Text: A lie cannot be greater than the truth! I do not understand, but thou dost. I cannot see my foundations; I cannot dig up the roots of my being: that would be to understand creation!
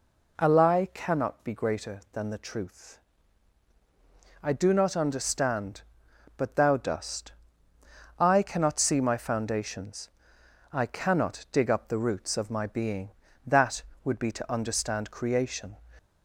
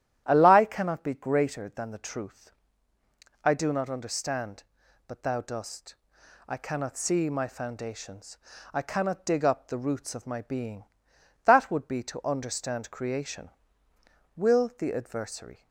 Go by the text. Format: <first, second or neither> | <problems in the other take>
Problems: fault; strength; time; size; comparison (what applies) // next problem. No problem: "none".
first | starts louder than the rest; strong; until 1.2 s; 11.5 dB // goes on to say "Will the Adversary"; from 14.3 s on; 1.3 s long